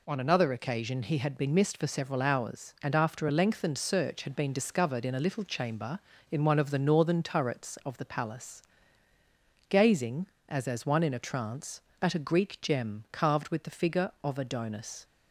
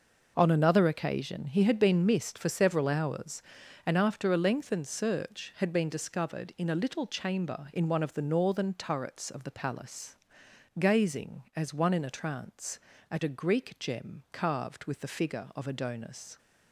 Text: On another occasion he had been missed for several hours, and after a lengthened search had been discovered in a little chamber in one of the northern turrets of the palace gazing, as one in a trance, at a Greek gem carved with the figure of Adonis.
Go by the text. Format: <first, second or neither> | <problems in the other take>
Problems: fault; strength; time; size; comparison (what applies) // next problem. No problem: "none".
second | pauses between "palace" and "gazing"; at 8.6 s; 1.0 s long; noticeable in the second // says "as" twice; at 10.6 s